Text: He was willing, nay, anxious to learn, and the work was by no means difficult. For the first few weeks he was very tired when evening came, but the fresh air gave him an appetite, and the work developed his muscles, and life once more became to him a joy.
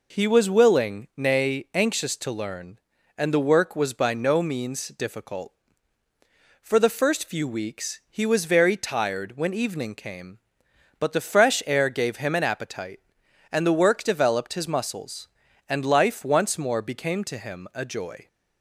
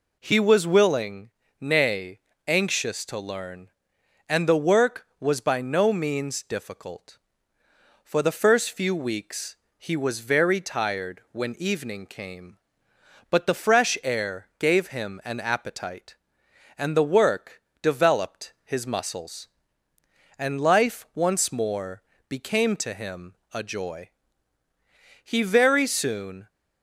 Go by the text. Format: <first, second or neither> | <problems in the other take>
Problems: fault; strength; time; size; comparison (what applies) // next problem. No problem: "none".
first | pauses between "weeks" and "he"; slight; at 9.5 s; 0.20 s long // pauses between "work" and "developed"; slight; at 17.6 s; 0.18 s long // pauses between "more" and "became"; slight; at 22.0 s; 0.26 s long // pauses between "him" and "a"; slight; at 23.3 s; 0.20 s long // goes on to say "He very soon"; noticeable; from 25.2 s on; 1.2 s long